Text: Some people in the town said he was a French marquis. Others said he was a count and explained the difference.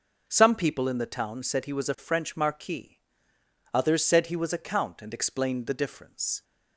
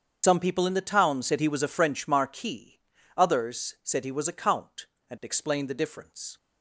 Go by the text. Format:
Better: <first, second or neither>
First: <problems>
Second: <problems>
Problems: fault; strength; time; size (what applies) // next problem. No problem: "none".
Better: first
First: none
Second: loses the start of "Some"; at 0.2 s; 70 ms // starts louder than the rest; strong; until 1.2 s; 7.5 dB